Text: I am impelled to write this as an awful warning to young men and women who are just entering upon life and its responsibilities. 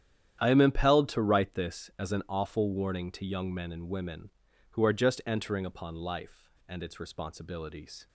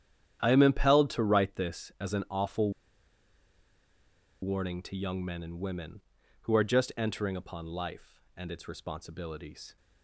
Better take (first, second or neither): first